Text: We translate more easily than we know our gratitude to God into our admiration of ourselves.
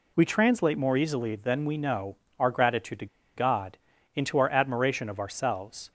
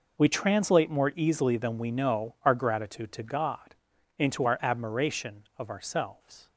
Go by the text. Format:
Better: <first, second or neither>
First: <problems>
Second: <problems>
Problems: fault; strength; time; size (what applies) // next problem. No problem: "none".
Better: second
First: pauses between "know" and "our"; slight; at 2.1 s; 0.20 s long // pauses between "to" and "God"; slight; at 3.0 s; 0.30 s long // pauses between "God" and "into"; at 3.7 s; 0.38 s long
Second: pauses between "God" and "into"; at 3.7 s; 0.42 s long